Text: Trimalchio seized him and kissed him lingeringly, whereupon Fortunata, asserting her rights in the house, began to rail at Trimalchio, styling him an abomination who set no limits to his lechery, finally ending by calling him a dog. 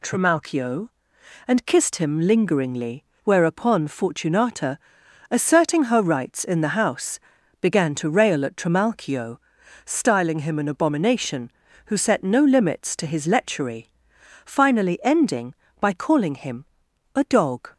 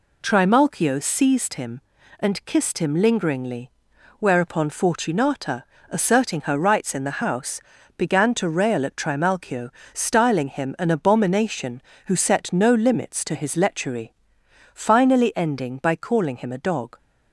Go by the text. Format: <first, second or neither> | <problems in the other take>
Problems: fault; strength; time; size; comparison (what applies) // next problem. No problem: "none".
second | skips "seized him"; at 1.1 s // pauses between "him" and "a"; noticeable; at 16.6 s; 0.50 s long